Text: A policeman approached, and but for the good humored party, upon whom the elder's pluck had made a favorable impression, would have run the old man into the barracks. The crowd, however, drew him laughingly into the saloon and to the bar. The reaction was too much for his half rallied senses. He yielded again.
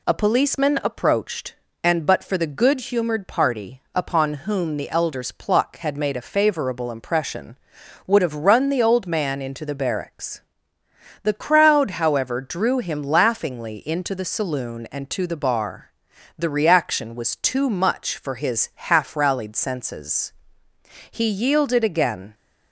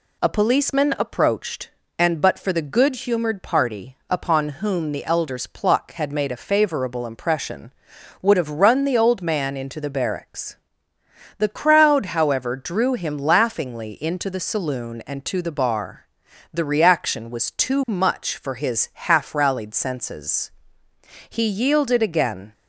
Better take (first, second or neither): neither